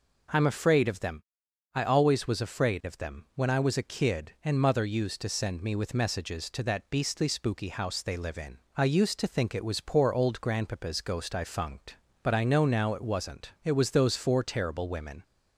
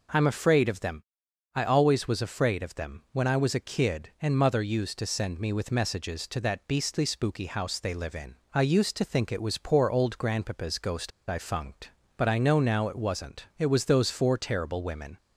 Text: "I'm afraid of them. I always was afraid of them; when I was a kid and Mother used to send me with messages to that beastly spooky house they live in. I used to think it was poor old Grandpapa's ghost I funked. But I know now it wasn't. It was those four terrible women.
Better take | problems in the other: first | pauses between "ghost" and "I"; slight; at 11.1 s; 0.18 s long

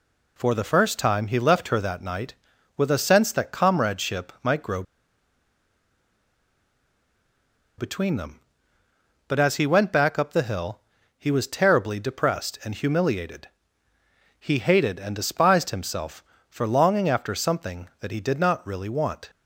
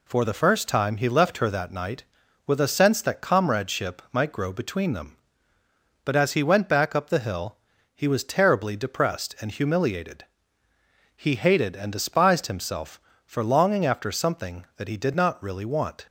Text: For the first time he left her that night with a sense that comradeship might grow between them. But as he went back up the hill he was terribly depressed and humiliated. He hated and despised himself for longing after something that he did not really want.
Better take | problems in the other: second | pauses between "grow" and "between"; strong; at 4.8 s; 2.9 s long // pauses between "hill" and "he"; slight; at 10.7 s; 0.36 s long; slight in the second

